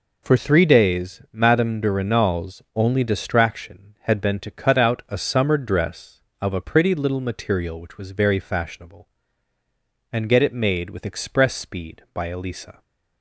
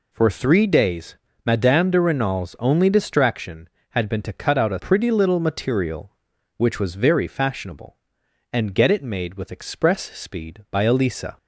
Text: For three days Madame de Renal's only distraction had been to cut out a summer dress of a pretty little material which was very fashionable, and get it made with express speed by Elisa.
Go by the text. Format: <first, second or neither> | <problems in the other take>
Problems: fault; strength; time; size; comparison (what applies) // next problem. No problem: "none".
first | pauses between "days" and "Madame"; slight; at 1.1 s; 0.28 s long // skips "summer dress of a"; at 4.7 s